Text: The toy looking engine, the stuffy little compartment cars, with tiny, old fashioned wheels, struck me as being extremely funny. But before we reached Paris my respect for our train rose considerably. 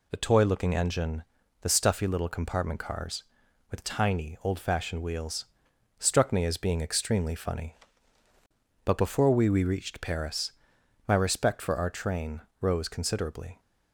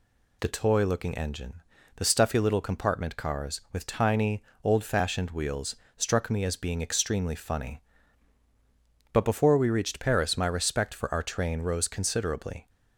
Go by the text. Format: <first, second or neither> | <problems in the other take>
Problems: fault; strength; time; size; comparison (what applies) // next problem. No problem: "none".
second | says "we" twice; at 9.4 s // pauses between "Paris" and "my"; noticeable; at 10.5 s; 0.56 s long // pauses between "train" and "rose"; slight; at 12.4 s; 0.20 s long